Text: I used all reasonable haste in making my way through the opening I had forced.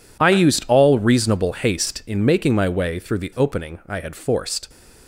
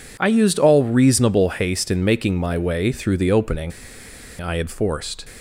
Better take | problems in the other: first | pauses between "opening" and "I"; noticeable; at 3.7 s; 0.69 s long

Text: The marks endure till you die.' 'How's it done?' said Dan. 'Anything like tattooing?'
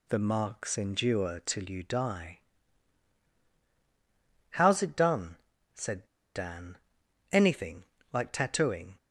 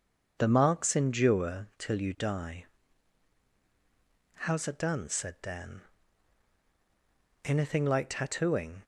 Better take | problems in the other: second | pauses between "said" and "Dan"; slight; at 6.0 s; 0.30 s long // pauses between "Anything" and "like"; slight; at 7.8 s; 0.26 s long

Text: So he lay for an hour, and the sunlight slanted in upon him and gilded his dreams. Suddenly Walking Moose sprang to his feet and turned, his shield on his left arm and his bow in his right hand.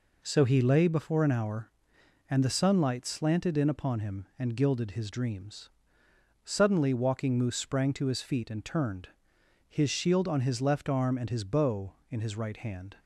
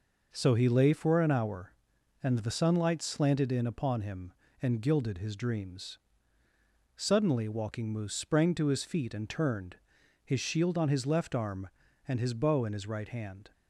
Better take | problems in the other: second | says "before" for "for"; at 0.8 s

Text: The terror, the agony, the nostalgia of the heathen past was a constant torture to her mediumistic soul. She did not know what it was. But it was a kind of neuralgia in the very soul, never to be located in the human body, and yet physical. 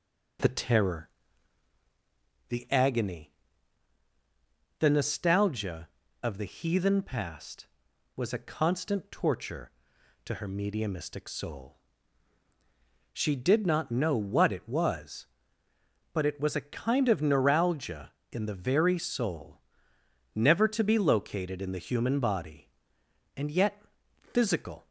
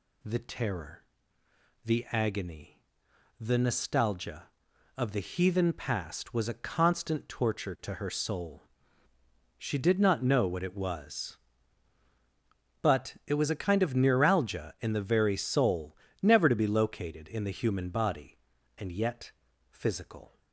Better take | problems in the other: first | skips "mediumistic"; at 8.0 s // pauses between "yet" and "physical"; at 19.3 s; 0.40 s long; noticeable in the first

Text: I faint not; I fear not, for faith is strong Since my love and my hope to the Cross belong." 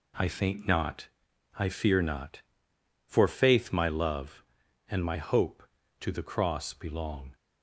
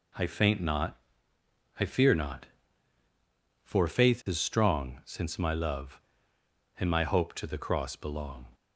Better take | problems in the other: second | skips "is strong Since"; at 3.7 s

